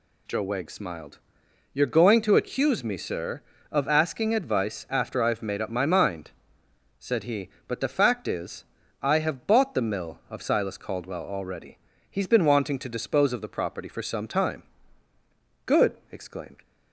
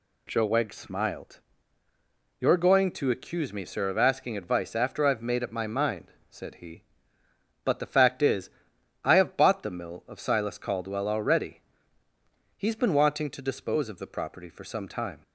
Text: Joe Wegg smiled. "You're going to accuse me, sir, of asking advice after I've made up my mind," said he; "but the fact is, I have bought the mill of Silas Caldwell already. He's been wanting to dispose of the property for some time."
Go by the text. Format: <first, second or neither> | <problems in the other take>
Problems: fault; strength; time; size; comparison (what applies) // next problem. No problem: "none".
second | goes on to say "Good exclaimed"; noticeable; from 15.6 s on; 0.98 s long